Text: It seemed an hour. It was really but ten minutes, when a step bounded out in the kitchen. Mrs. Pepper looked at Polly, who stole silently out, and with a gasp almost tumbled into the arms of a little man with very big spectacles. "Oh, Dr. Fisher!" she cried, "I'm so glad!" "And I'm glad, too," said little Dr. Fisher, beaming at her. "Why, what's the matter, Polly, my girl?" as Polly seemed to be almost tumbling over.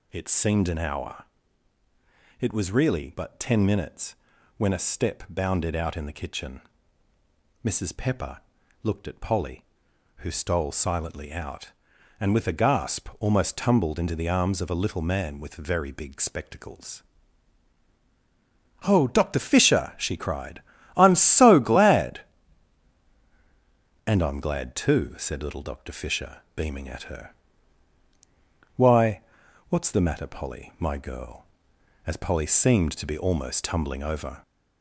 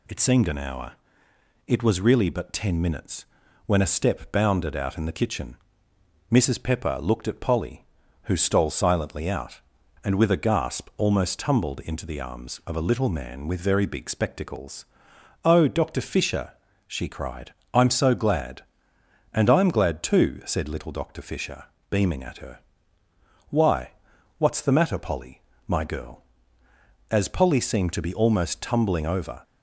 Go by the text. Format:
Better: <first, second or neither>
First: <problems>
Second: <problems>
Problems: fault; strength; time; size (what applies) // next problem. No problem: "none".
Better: second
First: gets louder; slight; throughout; 2 dB // pauses between "Pepper" and "looked"; at 8.3 s; 0.44 s long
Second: none